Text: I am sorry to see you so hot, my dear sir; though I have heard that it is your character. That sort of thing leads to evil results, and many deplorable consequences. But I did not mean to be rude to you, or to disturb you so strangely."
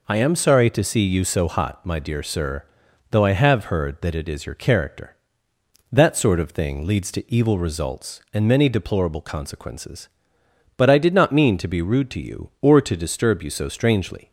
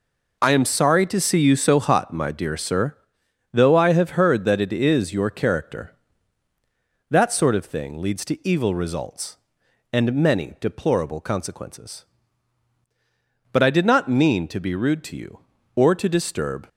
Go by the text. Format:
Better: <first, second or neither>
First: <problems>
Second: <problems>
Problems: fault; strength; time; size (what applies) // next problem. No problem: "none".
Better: first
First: none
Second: stops before "you so strangely"; at 16.6 s